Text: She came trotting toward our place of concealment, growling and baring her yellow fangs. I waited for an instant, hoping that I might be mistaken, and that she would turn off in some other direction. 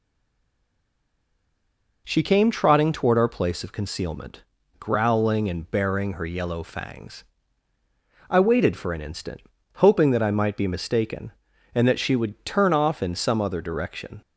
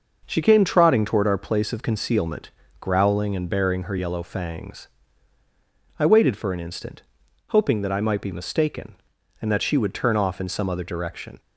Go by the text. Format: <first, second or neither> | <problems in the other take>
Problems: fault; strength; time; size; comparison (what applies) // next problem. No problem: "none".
second | stays silent before the first word; noticeable; until 2.0 s; 2.0 s long